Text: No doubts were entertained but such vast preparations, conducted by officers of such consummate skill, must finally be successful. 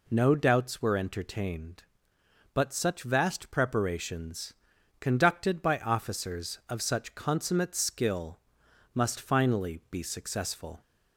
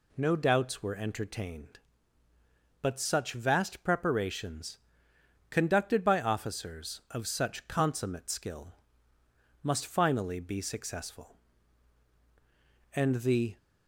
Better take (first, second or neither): first